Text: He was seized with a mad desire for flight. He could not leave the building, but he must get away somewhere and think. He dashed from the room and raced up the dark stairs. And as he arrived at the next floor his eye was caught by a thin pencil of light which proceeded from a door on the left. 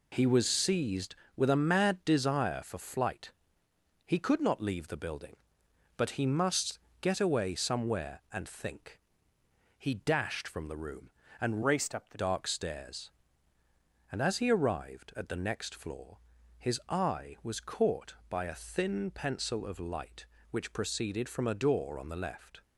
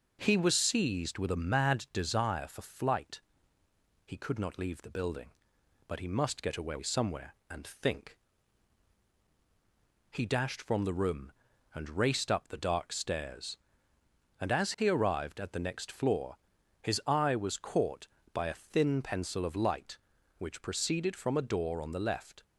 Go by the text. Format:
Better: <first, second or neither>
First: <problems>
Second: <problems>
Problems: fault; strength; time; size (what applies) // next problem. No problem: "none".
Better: second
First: pauses between "must" and "get"; slight; at 6.7 s; 0.24 s long // changes voice from "raced" to "the"; from 11.6 to 12.1 s; 0.5 s long // pauses between "floor" and "his"; at 16.1 s; 0.40 s long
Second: pauses between "floor" and "his"; at 16.3 s; 0.44 s long